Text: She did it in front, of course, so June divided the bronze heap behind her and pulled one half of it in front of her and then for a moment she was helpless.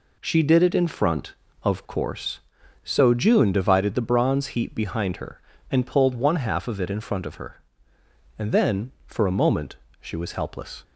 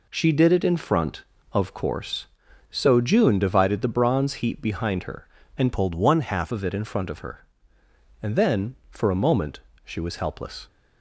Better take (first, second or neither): first